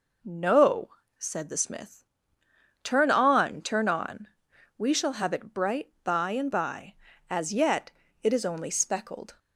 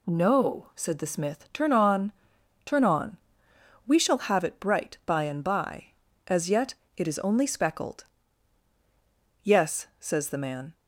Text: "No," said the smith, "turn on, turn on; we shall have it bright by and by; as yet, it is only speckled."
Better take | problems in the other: first | goes on to say "Yes says the man"; from 9.4 s on; 1.3 s long

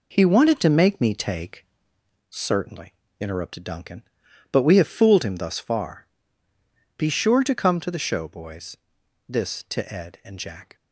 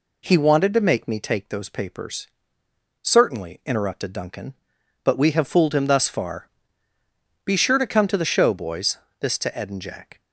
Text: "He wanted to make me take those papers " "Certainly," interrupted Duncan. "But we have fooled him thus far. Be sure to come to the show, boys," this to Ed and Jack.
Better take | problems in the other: second | skips "those papers"; at 1.8 s

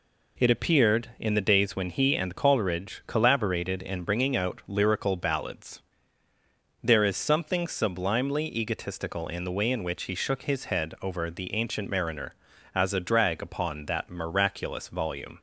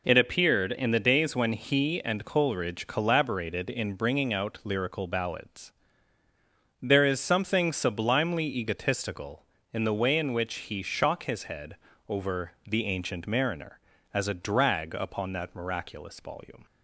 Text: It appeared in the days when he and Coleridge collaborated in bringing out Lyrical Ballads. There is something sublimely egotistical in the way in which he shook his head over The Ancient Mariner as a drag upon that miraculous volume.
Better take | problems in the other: first | says "shock" for "shook"; at 10.8 s // pauses between "head" and "over"; slight; at 11.7 s; 0.32 s long // pauses between "over" and "The"; slight; at 12.5 s; 0.16 s long

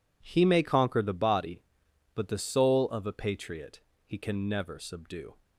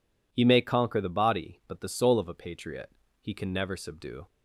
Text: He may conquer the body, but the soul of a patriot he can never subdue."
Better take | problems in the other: neither | pauses between "patriot" and "he"; slight; the same in both

